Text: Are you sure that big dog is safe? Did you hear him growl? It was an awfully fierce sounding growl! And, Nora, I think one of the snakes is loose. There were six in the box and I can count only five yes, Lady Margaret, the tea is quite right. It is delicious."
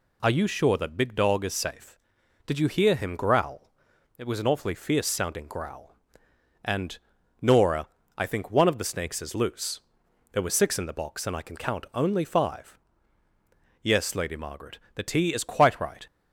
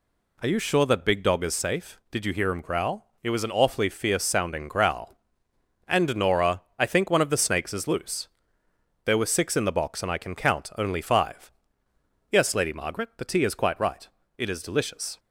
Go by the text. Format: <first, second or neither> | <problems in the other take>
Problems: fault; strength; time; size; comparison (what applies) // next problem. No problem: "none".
second | pauses between "five" and "yes"; at 12.7 s; 1.0 s long; noticeable in the second // stops before "It is delicious"; at 16.0 s